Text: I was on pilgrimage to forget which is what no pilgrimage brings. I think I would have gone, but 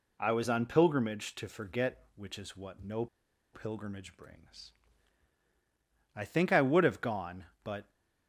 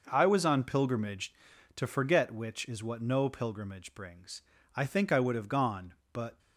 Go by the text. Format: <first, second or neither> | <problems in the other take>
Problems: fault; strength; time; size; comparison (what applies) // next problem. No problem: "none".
second | pauses between "no" and "pilgrimage"; noticeable; at 3.0 s; 0.47 s long